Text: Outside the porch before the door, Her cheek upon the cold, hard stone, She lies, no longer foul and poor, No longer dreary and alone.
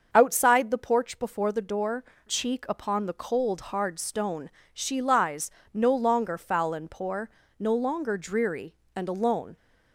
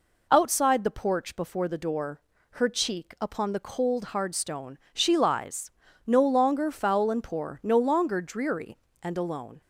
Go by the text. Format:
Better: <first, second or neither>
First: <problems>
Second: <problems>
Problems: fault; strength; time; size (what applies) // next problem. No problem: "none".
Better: second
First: starts louder than the rest; until 1.1 s; 6.5 dB // skips "Her"; at 2.1 s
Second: none